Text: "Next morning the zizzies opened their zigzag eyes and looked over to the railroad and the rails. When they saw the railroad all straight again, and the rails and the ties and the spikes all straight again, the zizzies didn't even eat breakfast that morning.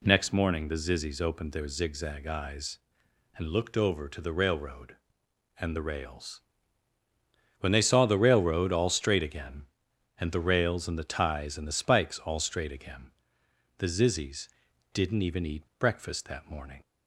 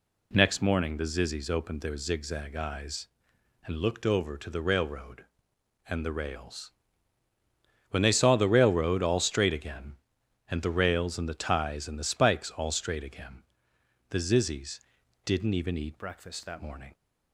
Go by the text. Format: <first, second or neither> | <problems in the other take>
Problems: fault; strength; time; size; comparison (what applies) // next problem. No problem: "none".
first | pauses between "zizzies" and "didn't"; noticeable; at 14.7 s; 0.46 s long; noticeable in the first // changes voice from "breakfast" to "that"; from 15.9 to 16.6 s; 0.7 s long